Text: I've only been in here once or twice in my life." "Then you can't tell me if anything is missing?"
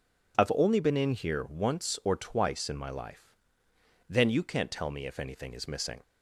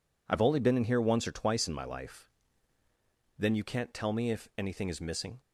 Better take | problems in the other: neither | none

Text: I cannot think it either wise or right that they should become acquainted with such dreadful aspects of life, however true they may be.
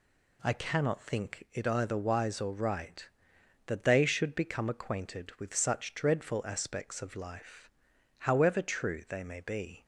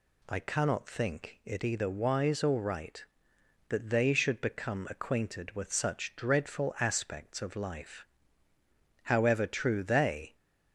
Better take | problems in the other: first | stops before "may be"; at 10.3 s

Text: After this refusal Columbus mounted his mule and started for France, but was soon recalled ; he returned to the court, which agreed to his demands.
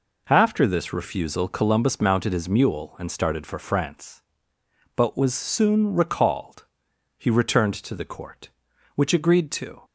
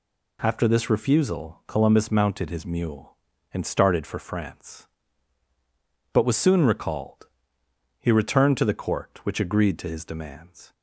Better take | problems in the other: second | stops before "his demands"; at 9.8 s

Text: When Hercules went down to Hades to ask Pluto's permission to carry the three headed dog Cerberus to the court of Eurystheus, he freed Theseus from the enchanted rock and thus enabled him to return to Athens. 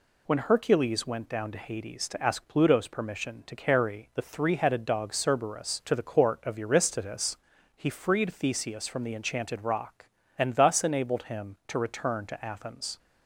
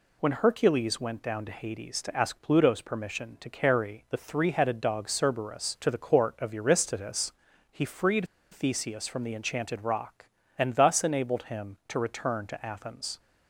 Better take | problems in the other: first | pauses between "freed" and "Theseus"; slight; at 8.2 s; 0.25 s long

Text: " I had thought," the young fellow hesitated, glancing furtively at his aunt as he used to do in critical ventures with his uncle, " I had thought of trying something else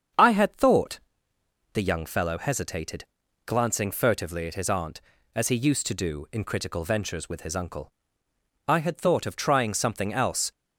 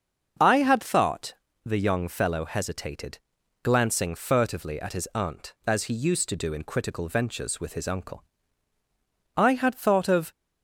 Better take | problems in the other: first | starts louder than the rest; until 1.7 s; 7 dB; strong in the first // stops before "trying something else"; at 10.3 s

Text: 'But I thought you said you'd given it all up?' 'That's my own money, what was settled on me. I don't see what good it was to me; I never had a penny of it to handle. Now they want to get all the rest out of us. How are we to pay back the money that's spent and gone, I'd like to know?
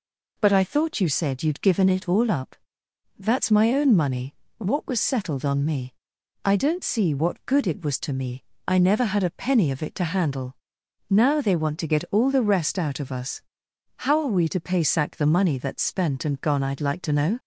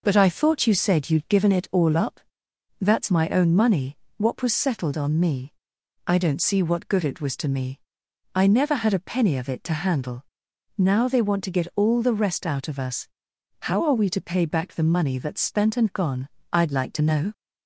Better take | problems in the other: second | says "sack" for "back"; at 14.8 s

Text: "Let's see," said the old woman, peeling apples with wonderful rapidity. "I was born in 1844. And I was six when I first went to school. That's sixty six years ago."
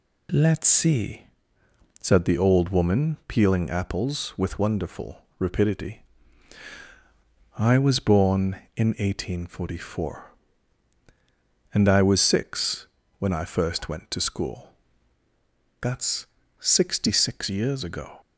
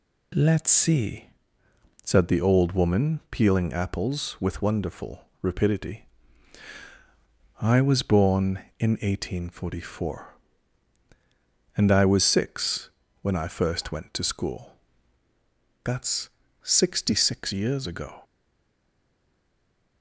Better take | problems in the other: first | pauses between "wonderful" and "rapidity"; slight; at 5.2 s; 0.18 s long; slight in the first // pauses between "six" and "when"; slight; at 12.8 s; 0.32 s long; slight in the first // pauses between "That's" and "sixty"; slight; at 16.2 s; 0.34 s long; slight in the first // stays silent after the last word; noticeable; from 18.2 s on; 1.8 s long

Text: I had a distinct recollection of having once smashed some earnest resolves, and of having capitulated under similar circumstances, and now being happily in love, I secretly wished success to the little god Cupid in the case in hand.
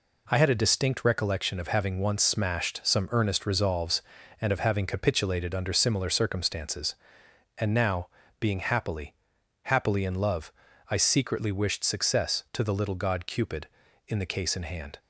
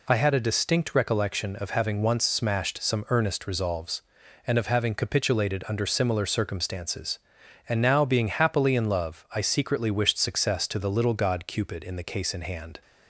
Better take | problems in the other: second | pauses between "now" and "being"; slight; at 8.0 s; 0.32 s long // says "happily" twice; at 9.6 s

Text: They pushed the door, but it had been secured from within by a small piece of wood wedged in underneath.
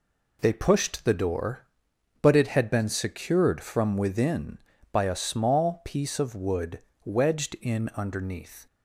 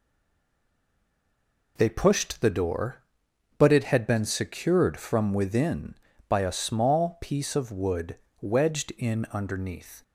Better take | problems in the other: first | stays silent before the first word; noticeable; until 1.7 s; 1.7 s long // pauses between "wood" and "wedged"; slight; at 8.1 s; 0.24 s long; slight in the first

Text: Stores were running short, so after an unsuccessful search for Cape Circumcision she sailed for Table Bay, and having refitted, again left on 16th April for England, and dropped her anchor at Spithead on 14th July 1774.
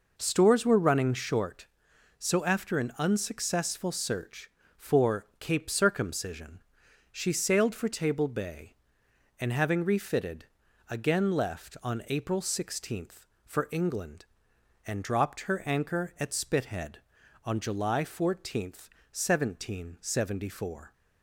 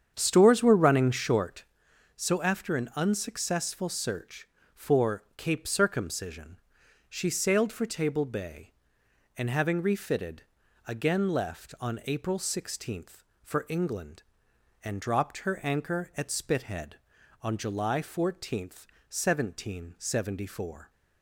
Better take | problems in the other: first | starts louder than the rest; strong; until 1.8 s; 8 dB // pauses between "Circumcision" and "she"; noticeable; at 6.5 s; 0.50 s long; noticeable in the first

